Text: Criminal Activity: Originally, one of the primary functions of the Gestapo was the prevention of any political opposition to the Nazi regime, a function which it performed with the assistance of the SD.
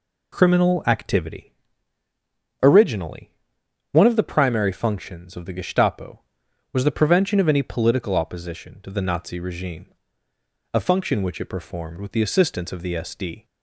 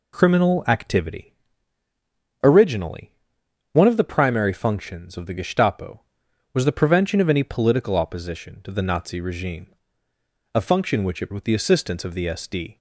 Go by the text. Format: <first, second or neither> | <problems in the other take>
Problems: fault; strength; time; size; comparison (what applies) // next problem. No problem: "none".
first | skips "performed"; at 11.3 s